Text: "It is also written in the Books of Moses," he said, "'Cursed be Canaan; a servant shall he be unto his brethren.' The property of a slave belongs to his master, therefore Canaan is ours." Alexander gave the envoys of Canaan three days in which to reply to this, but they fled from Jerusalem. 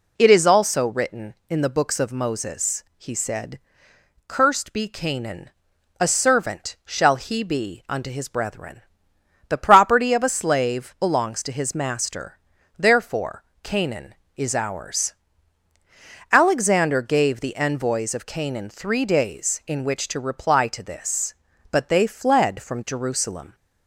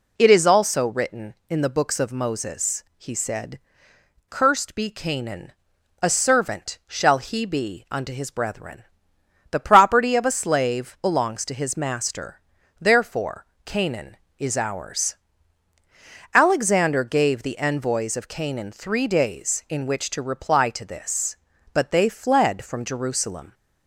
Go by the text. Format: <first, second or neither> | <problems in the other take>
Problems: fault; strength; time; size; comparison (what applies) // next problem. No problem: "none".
neither | pauses between "therefore" and "Canaan"; slight; the same in both